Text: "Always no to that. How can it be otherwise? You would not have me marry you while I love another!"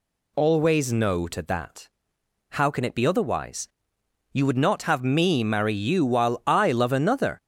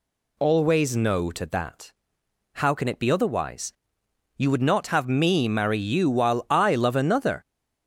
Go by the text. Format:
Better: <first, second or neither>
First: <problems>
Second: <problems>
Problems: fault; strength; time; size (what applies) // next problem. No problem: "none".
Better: neither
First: none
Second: none